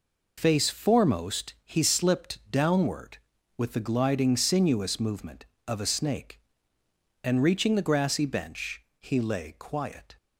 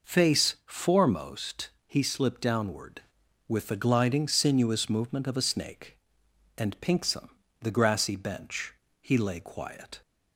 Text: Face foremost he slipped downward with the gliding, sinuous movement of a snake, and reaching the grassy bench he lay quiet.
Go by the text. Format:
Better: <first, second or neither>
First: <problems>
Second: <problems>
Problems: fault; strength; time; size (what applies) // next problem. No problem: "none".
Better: first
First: pauses between "bench" and "he"; slight; at 8.8 s; 0.20 s long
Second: pauses between "foremost" and "he"; slight; at 1.7 s; 0.16 s long // says "pinksome" for "reaching"; at 6.7 s // pauses between "bench" and "he"; slight; at 8.7 s; 0.28 s long